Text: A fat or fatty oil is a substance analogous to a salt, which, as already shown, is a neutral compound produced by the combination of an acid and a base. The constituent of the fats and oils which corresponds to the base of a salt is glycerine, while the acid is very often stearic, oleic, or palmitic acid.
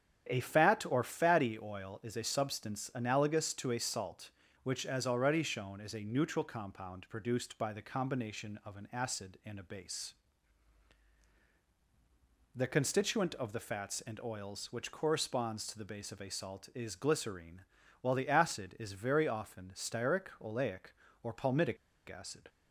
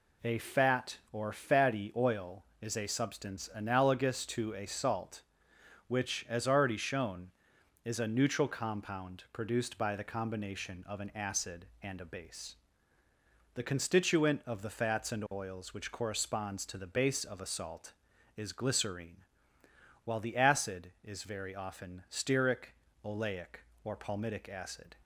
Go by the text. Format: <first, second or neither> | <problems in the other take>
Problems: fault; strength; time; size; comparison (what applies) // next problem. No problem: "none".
second | starts louder than the rest; strong; until 1.3 s; 9 dB // pauses between "palmitic" and "acid"; slight; at 21.7 s; 0.31 s long